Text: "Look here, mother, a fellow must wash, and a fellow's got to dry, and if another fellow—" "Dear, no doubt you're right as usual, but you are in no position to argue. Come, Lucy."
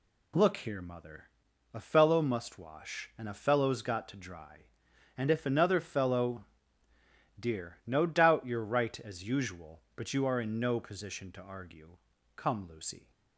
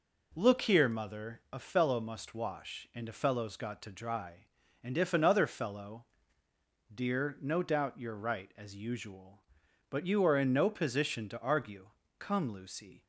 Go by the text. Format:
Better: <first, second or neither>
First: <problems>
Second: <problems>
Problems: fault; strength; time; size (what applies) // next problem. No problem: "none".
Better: neither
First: none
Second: none